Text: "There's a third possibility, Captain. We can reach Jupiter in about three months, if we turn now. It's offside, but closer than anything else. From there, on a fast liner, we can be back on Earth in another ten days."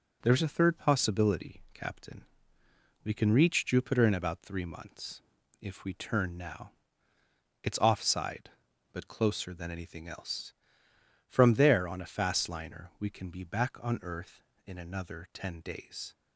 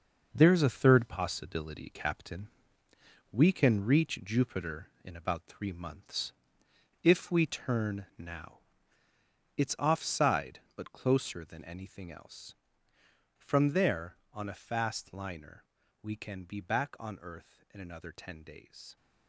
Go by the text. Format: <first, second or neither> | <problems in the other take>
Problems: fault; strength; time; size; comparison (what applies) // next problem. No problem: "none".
first | gets quieter; strong; throughout; 9 dB